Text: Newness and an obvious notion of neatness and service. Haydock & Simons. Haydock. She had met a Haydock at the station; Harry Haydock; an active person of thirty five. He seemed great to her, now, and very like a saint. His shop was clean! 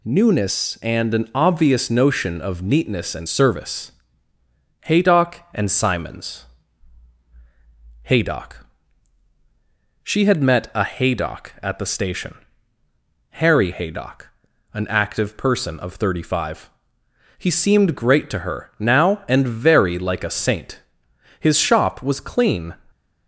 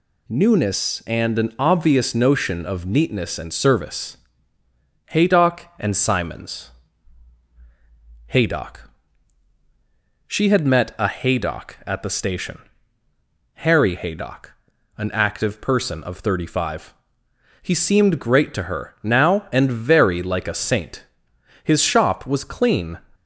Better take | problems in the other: neither | none

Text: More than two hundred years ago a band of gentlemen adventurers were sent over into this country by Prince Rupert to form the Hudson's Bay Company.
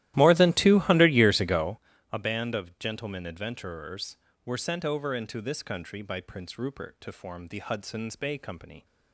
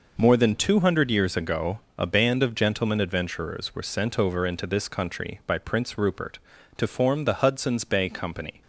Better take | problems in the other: second | starts louder than the rest; strong; until 1.8 s; 14.5 dB // pauses between "ago" and "a"; slight; at 1.7 s; 0.34 s long; slight in the second

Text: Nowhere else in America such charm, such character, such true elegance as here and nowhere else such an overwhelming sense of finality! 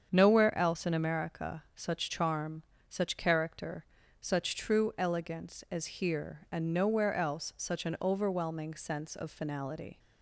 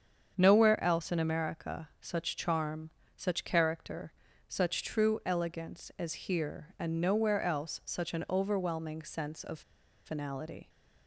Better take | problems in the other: first | starts louder than the rest; strong; until 1.3 s; 7.5 dB; strong in the first // pauses between "of" and "finality"; at 9.6 s; 0.44 s long

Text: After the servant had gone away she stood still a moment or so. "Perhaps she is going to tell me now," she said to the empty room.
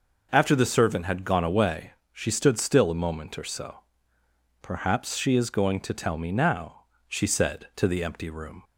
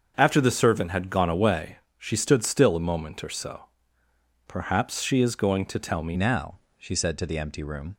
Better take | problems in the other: first | starts louder than the rest; until 1.1 s; 6.5 dB // pauses between "away" and "she"; slight; at 1.7 s; 0.20 s long; slight in the first // changes voice at "now"; from 6.1 s on; 1.8 s long

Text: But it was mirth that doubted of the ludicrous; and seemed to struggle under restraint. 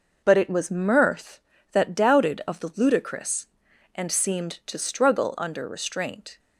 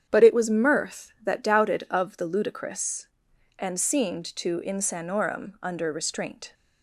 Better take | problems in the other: first | starts louder than the rest; strong; until 1.1 s; 8.5 dB // says "insanorum" for "struggle"; at 4.6 s

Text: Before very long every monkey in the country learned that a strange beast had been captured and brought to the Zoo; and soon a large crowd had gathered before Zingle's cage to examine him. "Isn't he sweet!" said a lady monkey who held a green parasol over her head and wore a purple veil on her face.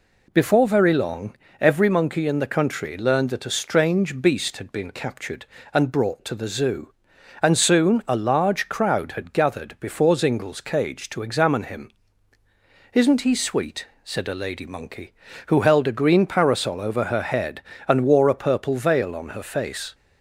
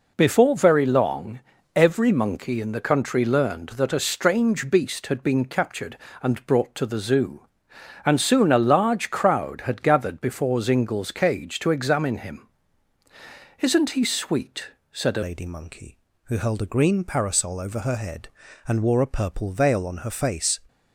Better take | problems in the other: first | pauses between "long" and "every"; slight; at 1.3 s; 0.36 s long; slight in the first // changes voice at "lady"; from 15.2 s on; 5.3 s long

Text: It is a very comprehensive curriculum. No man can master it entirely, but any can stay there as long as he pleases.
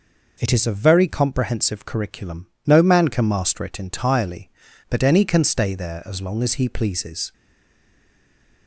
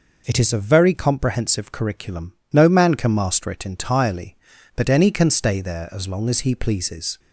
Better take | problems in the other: second | stays silent after the last word; noticeable; from 7.3 s on; 1.3 s long

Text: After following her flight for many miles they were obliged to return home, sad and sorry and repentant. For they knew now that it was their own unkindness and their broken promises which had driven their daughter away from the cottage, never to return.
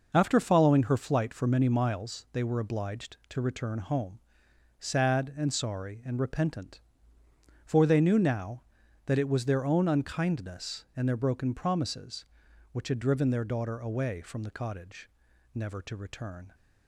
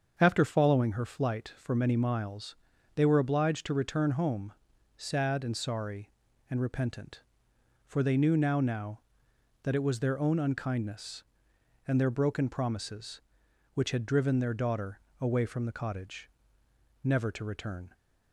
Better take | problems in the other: first | starts louder than the rest; until 1.2 s; 7 dB // pauses between "miles" and "they"; at 2.5 s; 0.40 s long // says "now" twice; at 8.5 s // pauses between "daughter" and "away"; slight; at 14.9 s; 0.20 s long

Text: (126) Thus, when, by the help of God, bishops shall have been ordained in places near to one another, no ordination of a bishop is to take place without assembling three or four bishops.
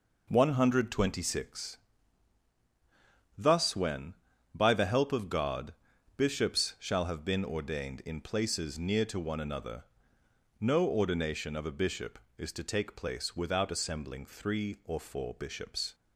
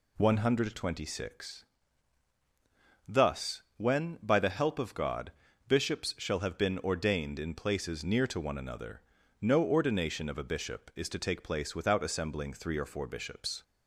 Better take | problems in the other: neither | none

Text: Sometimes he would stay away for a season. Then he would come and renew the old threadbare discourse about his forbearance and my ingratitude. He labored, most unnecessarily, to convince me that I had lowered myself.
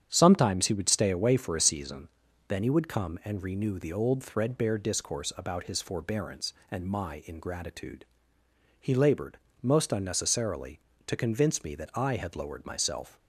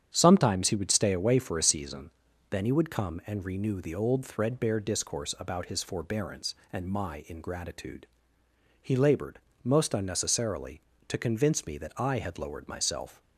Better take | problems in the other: neither | starts louder than the rest; strong; the same in both

